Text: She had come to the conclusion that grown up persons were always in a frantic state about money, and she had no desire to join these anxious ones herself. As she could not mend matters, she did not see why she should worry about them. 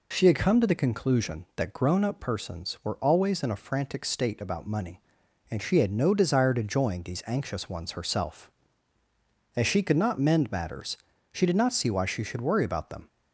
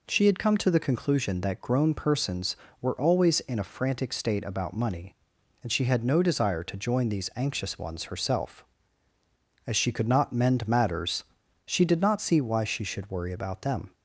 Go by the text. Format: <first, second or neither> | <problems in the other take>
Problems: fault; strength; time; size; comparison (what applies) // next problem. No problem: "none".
first | skips "up"; at 1.9 s